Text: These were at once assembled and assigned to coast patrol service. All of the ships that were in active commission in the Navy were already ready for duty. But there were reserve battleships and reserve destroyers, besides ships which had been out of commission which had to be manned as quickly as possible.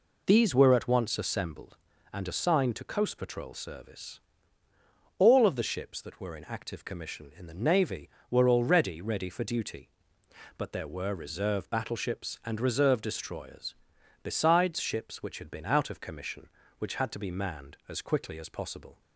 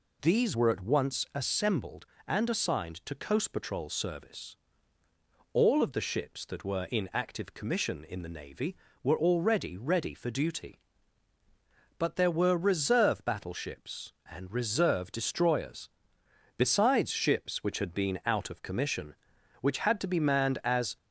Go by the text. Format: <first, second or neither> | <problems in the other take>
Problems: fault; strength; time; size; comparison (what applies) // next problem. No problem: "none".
first | stops before "quickly as possible"; at 20.9 s